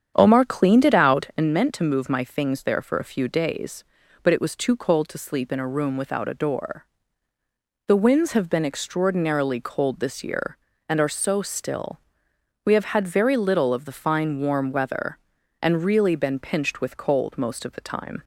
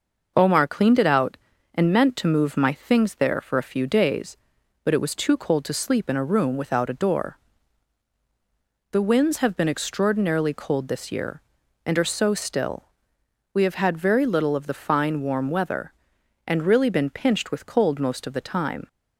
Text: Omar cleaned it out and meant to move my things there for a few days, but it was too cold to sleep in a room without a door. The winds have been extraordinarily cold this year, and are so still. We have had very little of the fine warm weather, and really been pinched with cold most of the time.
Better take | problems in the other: second | starts louder than the rest; strong; until 1.5 s; 8.5 dB

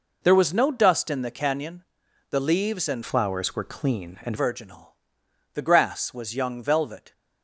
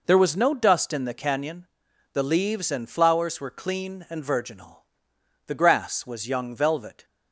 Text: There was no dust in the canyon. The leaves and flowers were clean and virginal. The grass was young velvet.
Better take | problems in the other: second | changes voice from "flowers" to "and"; from 3.0 to 4.3 s; 1.3 s long

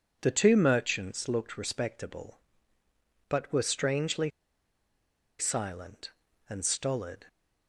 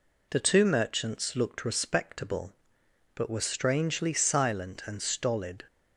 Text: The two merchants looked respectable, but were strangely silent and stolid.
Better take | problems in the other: second | pauses between "strangely" and "silent"; at 4.2 s; 1.0 s long

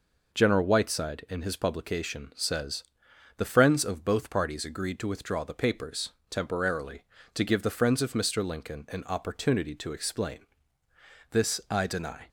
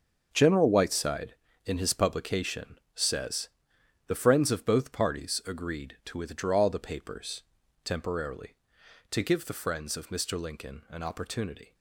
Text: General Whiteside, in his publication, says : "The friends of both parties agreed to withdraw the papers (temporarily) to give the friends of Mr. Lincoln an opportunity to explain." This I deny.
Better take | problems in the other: first | starts louder than the rest; until 1.3 s; 6.5 dB // stops before "to explain This I deny"; at 11.7 s

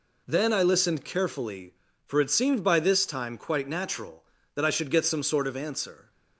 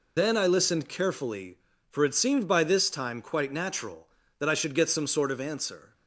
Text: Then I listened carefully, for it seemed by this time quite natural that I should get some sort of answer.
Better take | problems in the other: first | loses the start of "Then"; at 0.1 s; 65 ms

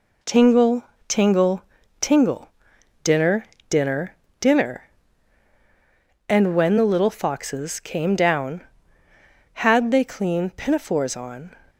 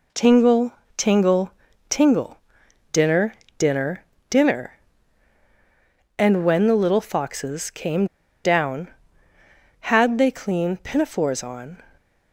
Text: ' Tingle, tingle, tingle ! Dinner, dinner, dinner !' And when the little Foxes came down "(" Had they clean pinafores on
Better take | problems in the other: first | pauses between "came" and "down"; at 8.0 s; 0.39 s long

